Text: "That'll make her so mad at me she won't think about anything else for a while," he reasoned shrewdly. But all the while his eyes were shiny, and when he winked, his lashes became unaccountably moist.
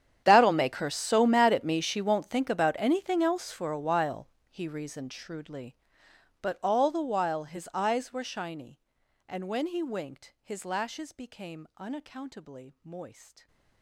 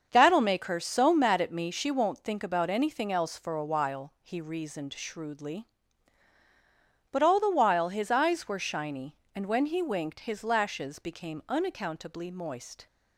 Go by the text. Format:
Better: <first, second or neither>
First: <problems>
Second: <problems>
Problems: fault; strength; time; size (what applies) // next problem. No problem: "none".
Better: second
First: gets quieter; strong; throughout; 22 dB // starts louder than the rest; strong; until 1.2 s; 9.5 dB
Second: starts louder than the rest; until 1.1 s; 6.5 dB